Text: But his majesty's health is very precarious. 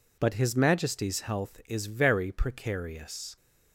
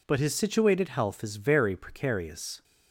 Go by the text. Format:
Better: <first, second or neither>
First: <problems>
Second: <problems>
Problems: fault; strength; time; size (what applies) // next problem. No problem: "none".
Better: first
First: none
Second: says "situated" for "majesty's"; at 0.3 s